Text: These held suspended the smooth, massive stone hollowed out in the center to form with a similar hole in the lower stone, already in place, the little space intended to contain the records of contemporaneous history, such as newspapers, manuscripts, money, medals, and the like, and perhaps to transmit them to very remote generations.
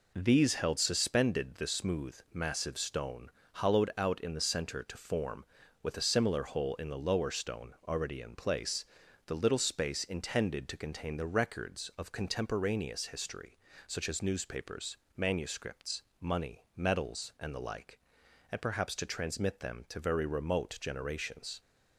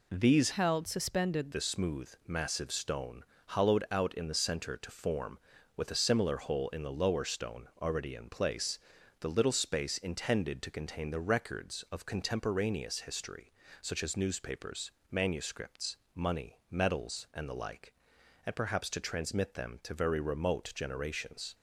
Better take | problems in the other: first | changes voice from "held" to "suspended"; from 0.5 to 1.5 s; 1.0 s long // pauses between "stone" and "hollowed"; slight; at 3.2 s; 0.22 s long; slight in the first

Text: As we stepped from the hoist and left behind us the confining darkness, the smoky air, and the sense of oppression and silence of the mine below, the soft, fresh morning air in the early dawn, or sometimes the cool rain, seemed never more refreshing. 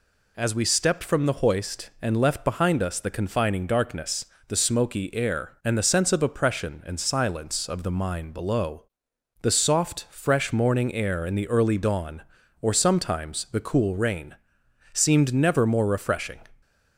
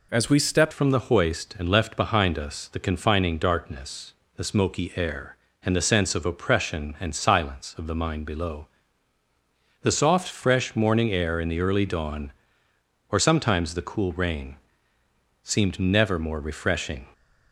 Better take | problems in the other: first | changes voice at "from"; from 0.7 s on; 16.3 s long

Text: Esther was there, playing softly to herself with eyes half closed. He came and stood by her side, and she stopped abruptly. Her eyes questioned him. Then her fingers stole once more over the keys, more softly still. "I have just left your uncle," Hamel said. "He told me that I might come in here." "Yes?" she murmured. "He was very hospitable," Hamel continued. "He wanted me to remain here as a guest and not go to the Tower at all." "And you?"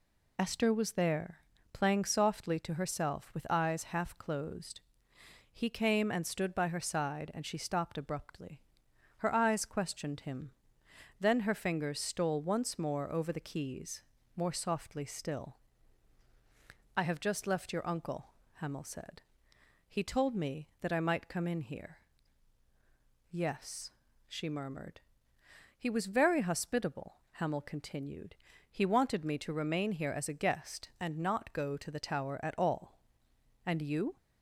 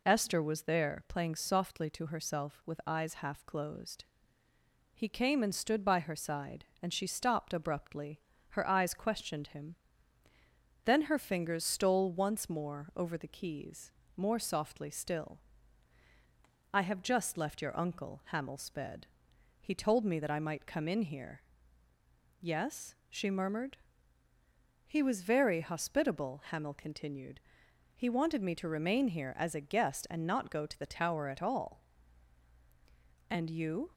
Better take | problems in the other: first | says "sped" for "said"; at 18.5 s

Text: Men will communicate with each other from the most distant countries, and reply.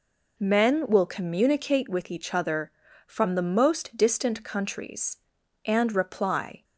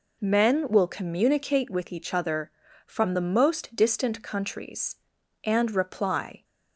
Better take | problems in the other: neither | none

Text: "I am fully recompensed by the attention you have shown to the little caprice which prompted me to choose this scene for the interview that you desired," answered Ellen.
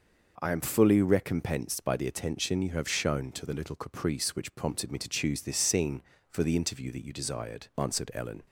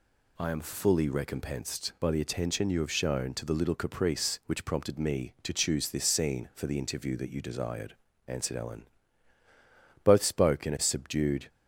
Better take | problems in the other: first | goes on to say "Both spoke in a subdued"; from 10.0 s on; 1.4 s long

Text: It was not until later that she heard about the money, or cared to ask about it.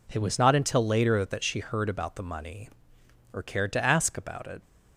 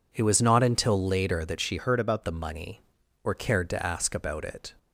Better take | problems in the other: first | changes voice from "heard" to "about"; from 1.7 to 2.2 s; 0.5 s long

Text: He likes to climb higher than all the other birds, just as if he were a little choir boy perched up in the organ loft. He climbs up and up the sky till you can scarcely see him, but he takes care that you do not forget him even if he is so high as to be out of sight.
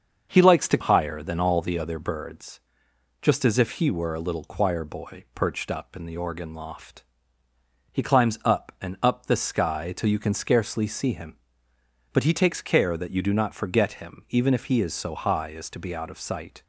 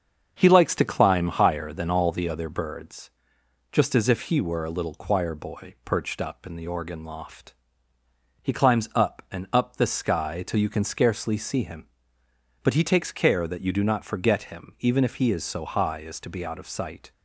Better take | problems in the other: second | starts louder than the rest; until 1.3 s; 6.5 dB; also in the second // skips "climb"; at 0.7 s

